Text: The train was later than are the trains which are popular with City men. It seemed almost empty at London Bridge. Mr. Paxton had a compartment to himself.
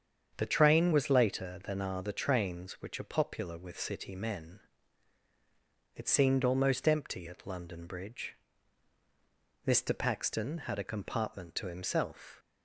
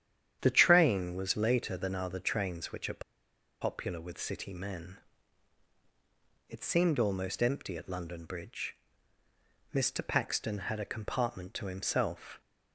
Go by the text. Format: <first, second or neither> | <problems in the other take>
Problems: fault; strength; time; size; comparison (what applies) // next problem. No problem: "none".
first | starts louder than the rest; strong; until 1.4 s; 9.5 dB; strong in the first // pauses between "are" and "popular"; noticeable; at 3.0 s; 0.61 s long